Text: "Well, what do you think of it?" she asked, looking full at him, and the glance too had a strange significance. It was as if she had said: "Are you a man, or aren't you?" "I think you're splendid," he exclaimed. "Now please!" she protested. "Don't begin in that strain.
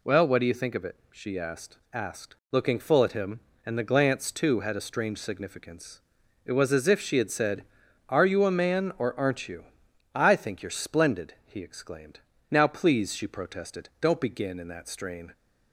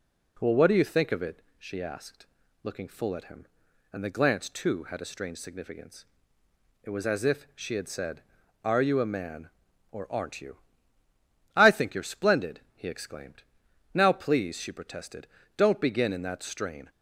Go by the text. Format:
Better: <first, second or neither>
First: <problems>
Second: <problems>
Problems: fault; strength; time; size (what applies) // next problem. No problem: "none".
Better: second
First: says "asked" twice; at 1.9 s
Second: none